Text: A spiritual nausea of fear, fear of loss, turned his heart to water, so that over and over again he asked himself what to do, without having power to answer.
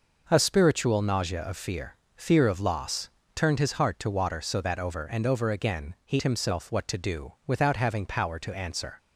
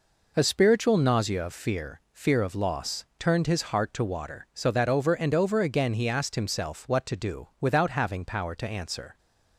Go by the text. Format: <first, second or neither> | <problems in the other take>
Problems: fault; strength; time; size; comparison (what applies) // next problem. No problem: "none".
second | skips "asked"; at 6.2 s